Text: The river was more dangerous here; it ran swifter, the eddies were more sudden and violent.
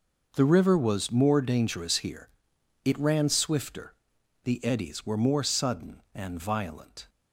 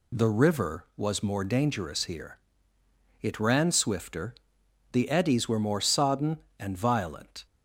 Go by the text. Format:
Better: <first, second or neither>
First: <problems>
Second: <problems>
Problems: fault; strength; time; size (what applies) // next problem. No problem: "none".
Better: first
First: none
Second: says "sodden" for "sudden"; at 5.8 s